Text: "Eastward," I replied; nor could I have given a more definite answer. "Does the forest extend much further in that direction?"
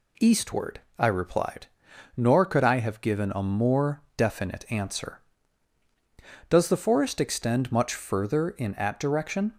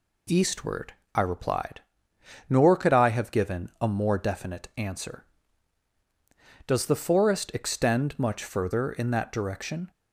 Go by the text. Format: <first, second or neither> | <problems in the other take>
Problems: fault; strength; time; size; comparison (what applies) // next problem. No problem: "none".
second | pauses between "more" and "definite"; slight; at 4.0 s; 0.16 s long // says "at" for "that"; at 8.7 s